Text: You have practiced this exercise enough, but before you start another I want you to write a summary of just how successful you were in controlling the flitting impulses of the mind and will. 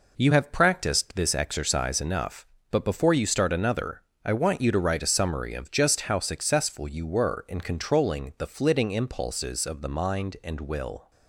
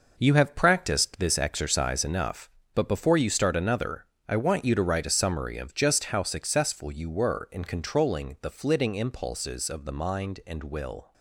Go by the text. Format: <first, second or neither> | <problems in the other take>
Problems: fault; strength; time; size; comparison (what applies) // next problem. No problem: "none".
first | gets quieter; strong; throughout; 8.5 dB // pauses between "another" and "I"; slight; at 4.0 s; 0.24 s long; slight in the first